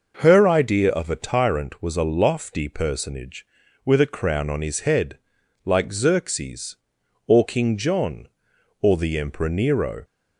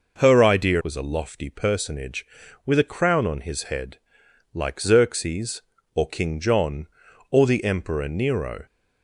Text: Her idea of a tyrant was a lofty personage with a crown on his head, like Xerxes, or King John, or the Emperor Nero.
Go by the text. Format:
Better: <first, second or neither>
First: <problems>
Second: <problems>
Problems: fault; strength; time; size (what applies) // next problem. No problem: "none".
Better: first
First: none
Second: skips "of a tyrant"; at 0.8 s